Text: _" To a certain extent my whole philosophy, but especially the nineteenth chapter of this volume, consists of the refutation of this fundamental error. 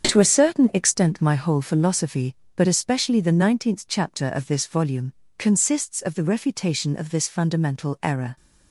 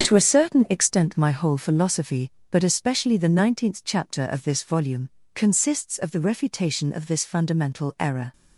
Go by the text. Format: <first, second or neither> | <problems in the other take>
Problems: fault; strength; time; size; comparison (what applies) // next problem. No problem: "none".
neither | starts louder than the rest; strong; the same in both